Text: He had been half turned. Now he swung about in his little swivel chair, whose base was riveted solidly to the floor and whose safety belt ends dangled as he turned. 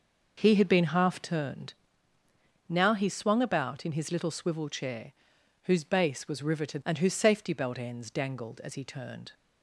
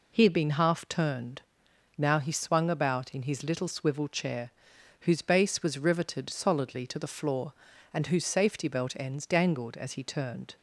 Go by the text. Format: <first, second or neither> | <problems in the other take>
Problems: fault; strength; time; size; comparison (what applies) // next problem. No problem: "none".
second | skips "solidly to the floor"; at 6.8 s